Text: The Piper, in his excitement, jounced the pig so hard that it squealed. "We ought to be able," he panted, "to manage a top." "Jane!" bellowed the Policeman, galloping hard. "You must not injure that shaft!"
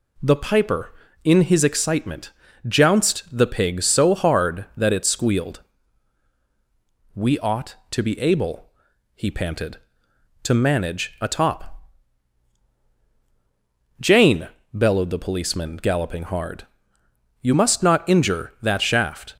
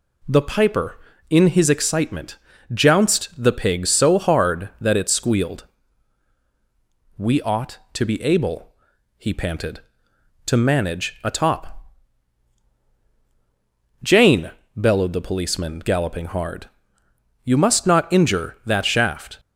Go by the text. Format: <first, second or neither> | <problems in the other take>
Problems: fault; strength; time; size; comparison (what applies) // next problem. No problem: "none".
neither | none